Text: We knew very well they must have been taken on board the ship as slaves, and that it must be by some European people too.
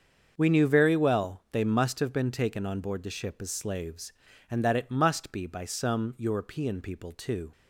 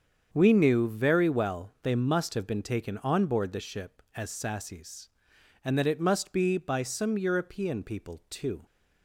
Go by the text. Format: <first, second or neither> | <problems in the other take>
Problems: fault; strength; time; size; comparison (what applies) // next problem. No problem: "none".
first | starts louder than the rest; strong; until 1.3 s; 7 dB; also in the first // says "sassies" for "slaves"; at 4.3 s